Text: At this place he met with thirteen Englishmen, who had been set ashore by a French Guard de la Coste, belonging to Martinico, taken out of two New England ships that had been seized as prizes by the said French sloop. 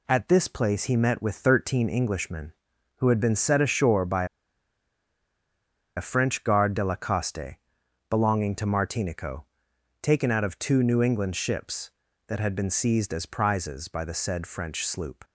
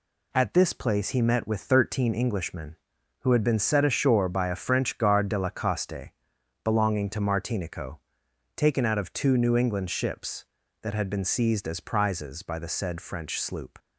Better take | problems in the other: second | pauses between "by" and "a"; strong; at 4.2 s; 1.7 s long

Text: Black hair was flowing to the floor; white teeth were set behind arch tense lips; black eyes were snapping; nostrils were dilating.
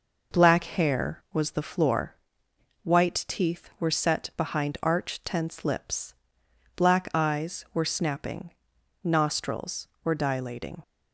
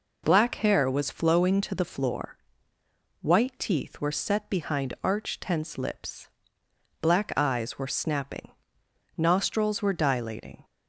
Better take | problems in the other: second | skips "flowing to"; at 1.5 s

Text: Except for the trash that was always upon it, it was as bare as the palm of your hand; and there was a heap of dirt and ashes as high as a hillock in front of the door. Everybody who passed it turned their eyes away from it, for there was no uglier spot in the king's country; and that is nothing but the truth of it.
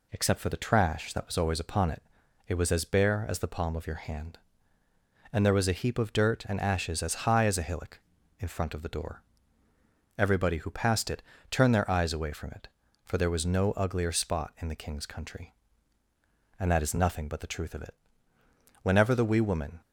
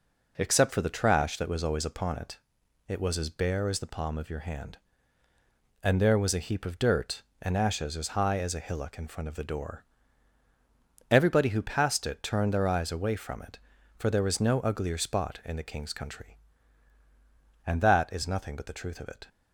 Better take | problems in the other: second | pauses between "it" and "turned"; slight; at 11.2 s; 0.30 s long // goes on to say "Whenever the wee woman"; noticeable; from 18.8 s on; 1.0 s long

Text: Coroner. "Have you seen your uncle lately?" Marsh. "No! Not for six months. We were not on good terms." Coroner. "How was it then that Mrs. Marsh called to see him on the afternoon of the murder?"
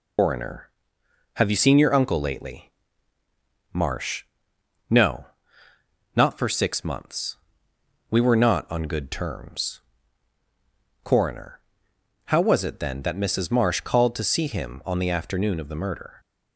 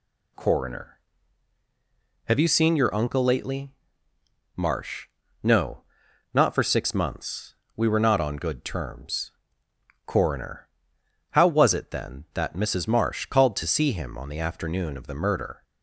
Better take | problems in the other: second | loses the start of "Coroner"; at 0.1 s; 150 ms

